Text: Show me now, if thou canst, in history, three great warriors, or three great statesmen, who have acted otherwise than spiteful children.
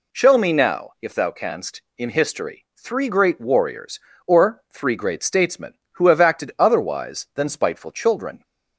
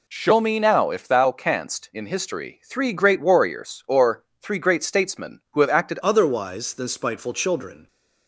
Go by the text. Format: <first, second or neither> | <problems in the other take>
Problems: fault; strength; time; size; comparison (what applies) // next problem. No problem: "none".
first | pauses between "or" and "three"; slight; at 4.2 s; 0.18 s long // changes voice at "otherwise"; from 6.0 s on; 1.8 s long